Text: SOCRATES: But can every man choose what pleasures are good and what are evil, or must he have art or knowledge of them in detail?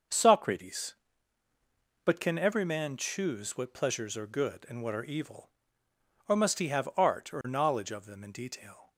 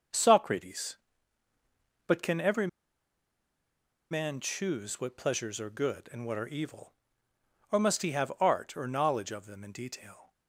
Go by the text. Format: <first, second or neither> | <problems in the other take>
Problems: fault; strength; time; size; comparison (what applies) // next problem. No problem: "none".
first | starts louder than the rest; noticeable; until 2.2 s; 6 dB; also in the first // pauses between "every" and "man"; strong; at 2.6 s; 1.4 s long